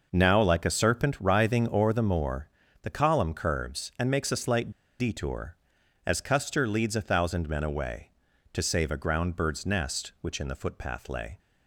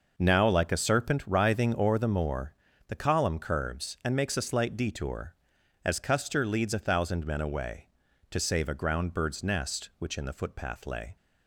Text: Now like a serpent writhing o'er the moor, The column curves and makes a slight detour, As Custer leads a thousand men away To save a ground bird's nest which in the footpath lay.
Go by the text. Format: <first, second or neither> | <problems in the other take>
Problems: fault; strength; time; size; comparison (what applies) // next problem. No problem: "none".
second | pauses between "slight" and "detour"; slight; at 4.7 s; 0.28 s long